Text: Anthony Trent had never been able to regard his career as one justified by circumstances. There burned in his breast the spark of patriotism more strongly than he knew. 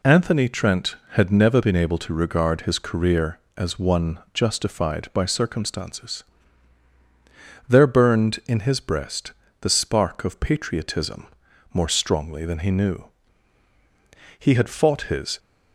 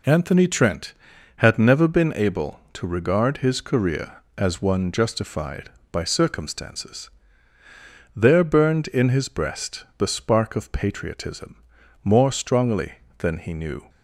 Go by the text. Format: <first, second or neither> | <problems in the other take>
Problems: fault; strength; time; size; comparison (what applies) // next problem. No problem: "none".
second | pauses between "one" and "justified"; slight; at 4.1 s; 0.16 s long // pauses between "breast" and "the"; slight; at 9.3 s; 0.28 s long // pauses between "patriotism" and "more"; noticeable; at 11.2 s; 0.46 s long; also in the second // goes on to say "He had fought his"; noticeable; from 14.4 s on; 0.98 s long